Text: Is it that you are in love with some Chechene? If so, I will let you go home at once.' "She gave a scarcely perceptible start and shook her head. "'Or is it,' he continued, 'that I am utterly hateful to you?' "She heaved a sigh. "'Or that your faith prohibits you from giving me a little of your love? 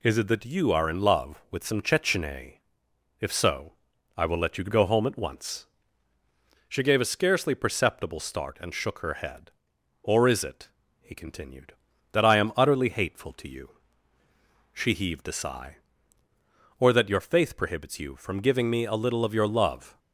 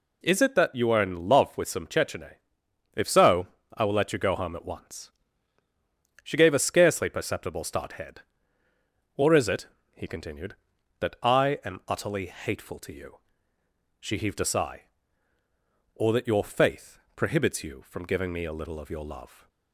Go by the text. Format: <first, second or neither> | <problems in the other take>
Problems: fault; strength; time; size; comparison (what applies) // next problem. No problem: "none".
first | skips "and shook her"; at 7.9 s // pauses between "faith" and "prohibits"; slight; at 17.0 s; 0.16 s long